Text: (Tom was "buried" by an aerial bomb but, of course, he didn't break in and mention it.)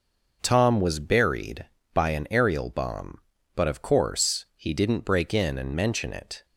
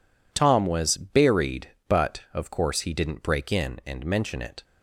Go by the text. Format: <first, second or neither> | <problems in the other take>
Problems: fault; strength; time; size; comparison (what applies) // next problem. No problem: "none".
first | skips "by an aerial bomb"; at 1.7 s